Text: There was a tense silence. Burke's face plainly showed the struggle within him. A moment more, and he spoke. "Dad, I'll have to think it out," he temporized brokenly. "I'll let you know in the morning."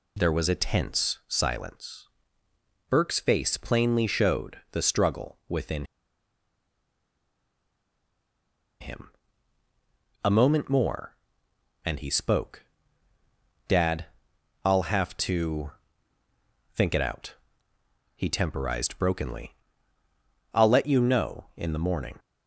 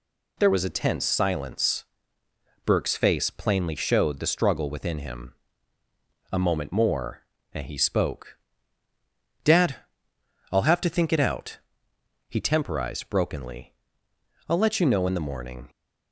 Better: second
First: pauses between "within" and "him"; strong; at 5.8 s; 2.9 s long // pauses between "to" and "think"; at 15.7 s; 1.0 s long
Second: none

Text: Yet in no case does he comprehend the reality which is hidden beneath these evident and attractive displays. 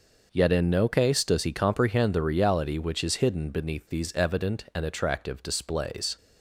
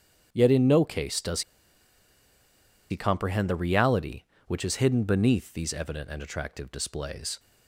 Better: first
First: none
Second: starts louder than the rest; strong; until 1.3 s; 8 dB // pauses between "does" and "he"; strong; at 1.4 s; 1.4 s long

